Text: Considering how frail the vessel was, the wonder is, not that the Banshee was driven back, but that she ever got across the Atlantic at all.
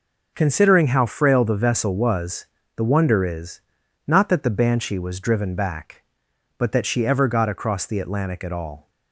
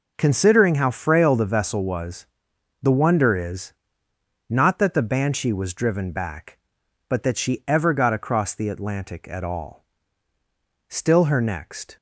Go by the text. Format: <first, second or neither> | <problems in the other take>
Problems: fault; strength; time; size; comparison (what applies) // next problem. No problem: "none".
first | goes on to say "Still her next"; noticeable; from 10.8 s on; 1.0 s long